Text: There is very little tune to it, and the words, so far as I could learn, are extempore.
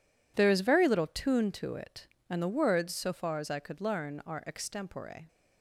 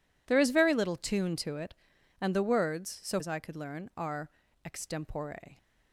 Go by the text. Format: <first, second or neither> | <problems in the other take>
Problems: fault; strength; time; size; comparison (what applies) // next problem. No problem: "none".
first | skips "far"; at 3.1 s // pauses between "are" and "extempore"; slight; at 4.2 s; 0.34 s long